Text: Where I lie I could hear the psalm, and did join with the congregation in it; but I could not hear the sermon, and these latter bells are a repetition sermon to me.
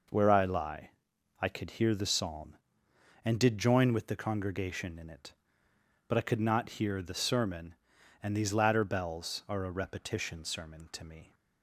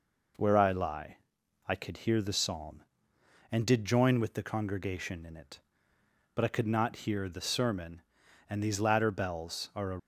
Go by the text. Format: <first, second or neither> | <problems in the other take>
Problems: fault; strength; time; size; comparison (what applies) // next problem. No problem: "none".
first | pauses between "lie" and "I"; noticeable; at 1.1 s; 0.50 s long; noticeable in the first // stops before "repetition sermon to me"; at 9.9 s